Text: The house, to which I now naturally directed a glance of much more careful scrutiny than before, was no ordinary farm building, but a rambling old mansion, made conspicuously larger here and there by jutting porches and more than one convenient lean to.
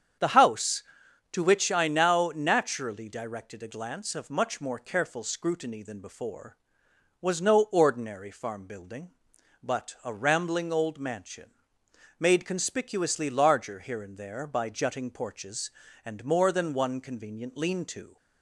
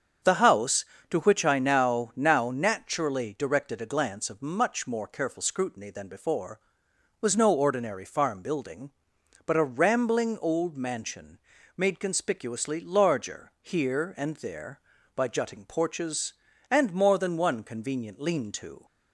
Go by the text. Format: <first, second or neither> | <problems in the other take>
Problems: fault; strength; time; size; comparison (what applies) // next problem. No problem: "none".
first | starts louder than the rest; until 1.4 s; 7 dB; strong in the first // says "now" twice; at 2.1 s